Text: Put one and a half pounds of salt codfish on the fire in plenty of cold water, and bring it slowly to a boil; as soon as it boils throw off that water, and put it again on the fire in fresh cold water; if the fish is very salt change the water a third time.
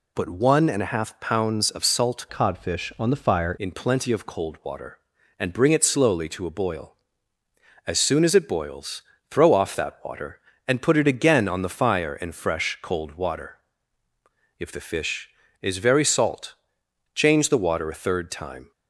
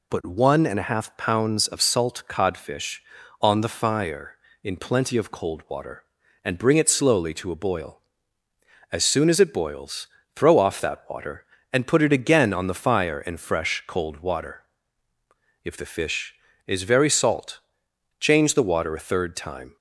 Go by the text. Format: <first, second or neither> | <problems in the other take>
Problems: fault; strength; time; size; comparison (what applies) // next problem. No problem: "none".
second | changes voice from "codfish" to "fire"; from 2.2 to 3.5 s; 1.3 s long // pauses between "boils" and "throw"; slight; at 9.0 s; 0.26 s long; slight in the second // pauses between "salt" and "change"; noticeable; at 16.5 s; 0.58 s long; noticeable in the second